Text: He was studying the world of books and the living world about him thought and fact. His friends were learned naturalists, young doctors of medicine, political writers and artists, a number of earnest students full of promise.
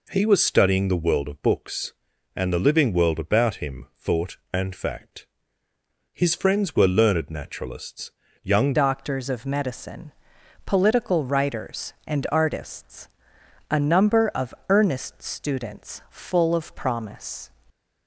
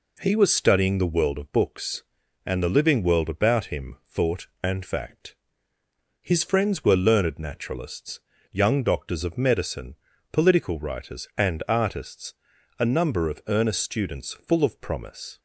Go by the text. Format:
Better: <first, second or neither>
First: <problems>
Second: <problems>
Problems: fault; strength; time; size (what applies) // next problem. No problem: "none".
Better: second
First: changes voice at "doctors"; from 8.7 s on; 8.8 s long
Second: none